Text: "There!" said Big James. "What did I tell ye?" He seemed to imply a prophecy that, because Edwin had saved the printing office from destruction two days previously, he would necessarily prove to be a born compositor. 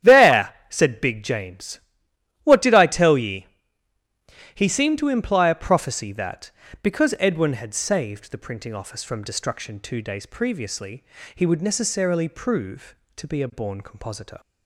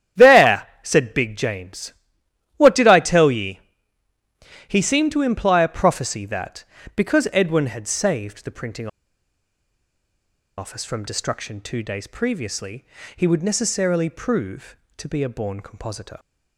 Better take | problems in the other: first | starts louder than the rest; strong; until 1.3 s; 10.5 dB; strong in the first // pauses between "printing" and "office"; strong; at 8.8 s; 1.7 s long

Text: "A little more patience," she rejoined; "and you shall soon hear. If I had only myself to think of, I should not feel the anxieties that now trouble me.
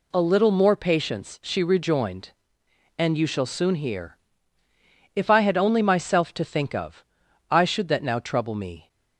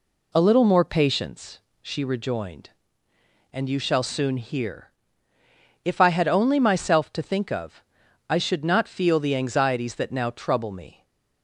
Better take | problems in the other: second | skips "not feel the anxieties"; at 7.8 s

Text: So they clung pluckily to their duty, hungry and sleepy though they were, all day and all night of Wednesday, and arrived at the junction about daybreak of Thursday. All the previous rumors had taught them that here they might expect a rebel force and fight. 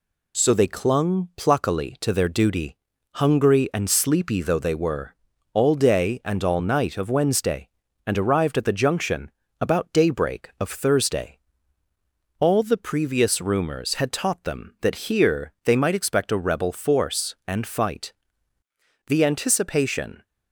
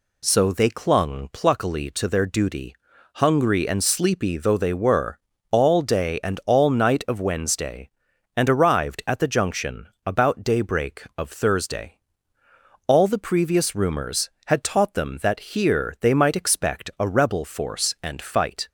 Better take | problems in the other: second | pauses between "junction" and "about"; slight; at 9.2 s; 0.32 s long; slight in the second // goes on to say "The anticipation"; noticeable; from 19.0 s on; 1.1 s long

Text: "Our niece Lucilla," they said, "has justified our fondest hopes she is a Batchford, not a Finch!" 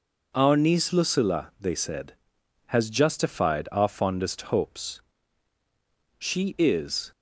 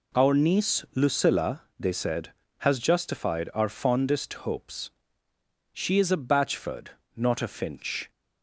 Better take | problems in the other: second | pauses between "hopes" and "she"; at 5.0 s; 1.1 s long; noticeable in the second // stops before "a Batchford not a Finch"; at 7.1 s

